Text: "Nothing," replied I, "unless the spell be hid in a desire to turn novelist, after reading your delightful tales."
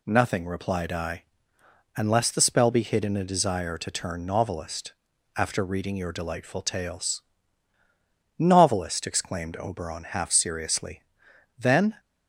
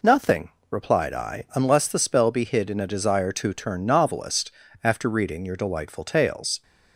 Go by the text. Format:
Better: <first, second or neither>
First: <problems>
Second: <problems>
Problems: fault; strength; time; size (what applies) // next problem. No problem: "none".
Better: second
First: goes on to say "Novelist exclaimed Oberon half seriously Then"; strong; from 8.3 s on; 3.6 s long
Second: none